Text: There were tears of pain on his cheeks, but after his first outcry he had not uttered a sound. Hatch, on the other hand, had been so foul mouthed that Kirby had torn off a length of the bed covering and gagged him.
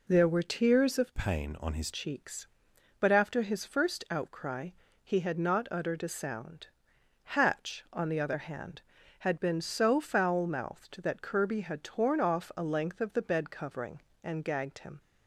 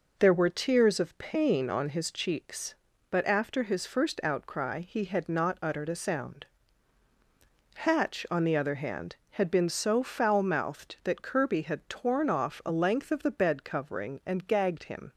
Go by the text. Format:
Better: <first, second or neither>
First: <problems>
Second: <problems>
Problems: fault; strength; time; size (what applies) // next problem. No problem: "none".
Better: second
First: changes voice from "pain" to "his"; from 1.1 to 1.9 s; 0.8 s long // pauses between "outcry" and "he"; slight; at 4.7 s; 0.34 s long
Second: none